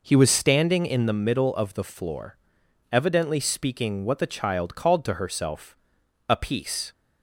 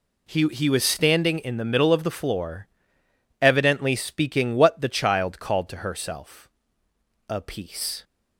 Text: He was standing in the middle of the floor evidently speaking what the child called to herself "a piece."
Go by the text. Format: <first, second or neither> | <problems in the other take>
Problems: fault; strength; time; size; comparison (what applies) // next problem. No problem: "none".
first | says "He" twice; at 0.4 s // pauses between "floor" and "evidently"; noticeable; at 2.6 s; 0.72 s long; noticeable in the first // pauses between "herself" and "a"; noticeable; at 6.4 s; 0.80 s long; noticeable in the first